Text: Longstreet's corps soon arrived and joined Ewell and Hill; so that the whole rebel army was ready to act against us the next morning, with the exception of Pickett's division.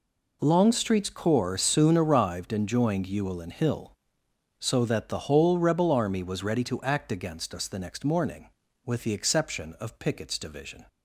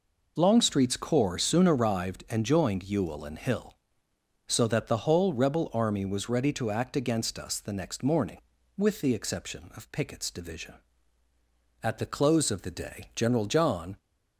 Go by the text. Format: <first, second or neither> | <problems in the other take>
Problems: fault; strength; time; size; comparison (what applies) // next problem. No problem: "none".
first | goes on to say "At the close of the day General John"; strong; from 11.8 s on; 2.1 s long